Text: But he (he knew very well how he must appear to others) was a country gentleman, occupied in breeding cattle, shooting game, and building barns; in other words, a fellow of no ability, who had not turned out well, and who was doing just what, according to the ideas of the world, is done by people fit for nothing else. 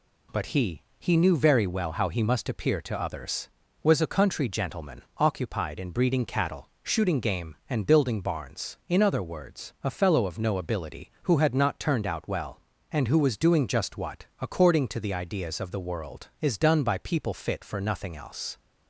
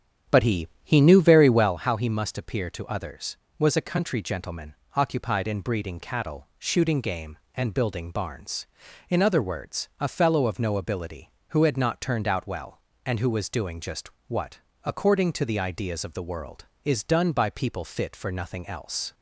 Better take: first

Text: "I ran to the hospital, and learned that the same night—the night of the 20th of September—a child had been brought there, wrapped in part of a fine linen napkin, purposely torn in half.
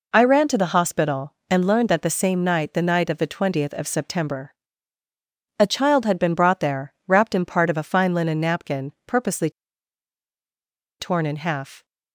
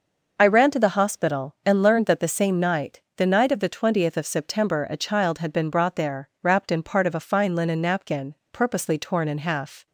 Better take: second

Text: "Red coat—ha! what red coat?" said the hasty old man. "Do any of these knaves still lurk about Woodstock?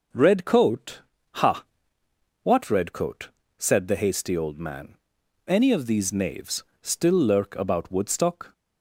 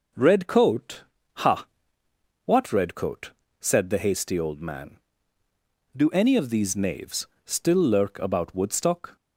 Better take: second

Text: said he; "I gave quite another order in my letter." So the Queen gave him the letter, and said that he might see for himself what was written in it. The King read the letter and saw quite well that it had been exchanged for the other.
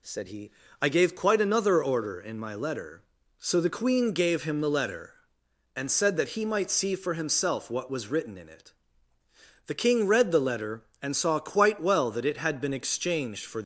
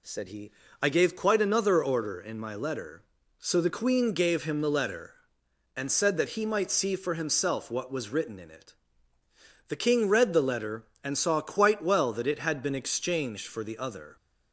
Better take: second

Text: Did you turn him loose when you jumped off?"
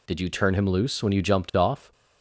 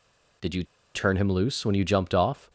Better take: first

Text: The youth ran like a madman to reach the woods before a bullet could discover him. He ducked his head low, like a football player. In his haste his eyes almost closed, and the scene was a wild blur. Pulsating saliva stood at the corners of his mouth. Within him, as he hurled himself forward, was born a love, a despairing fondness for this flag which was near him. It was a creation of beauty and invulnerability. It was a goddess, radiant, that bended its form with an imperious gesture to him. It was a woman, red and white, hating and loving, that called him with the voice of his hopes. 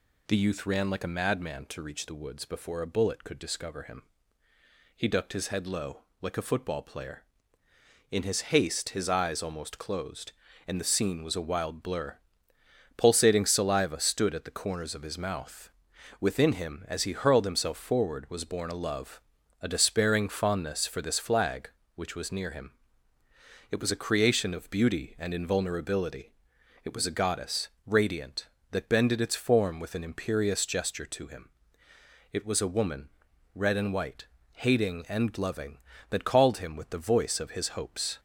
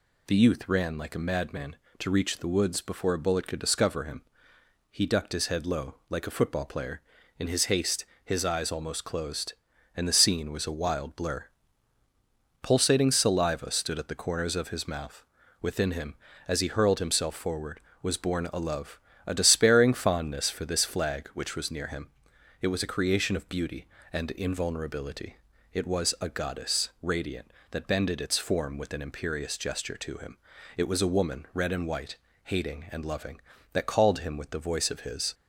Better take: first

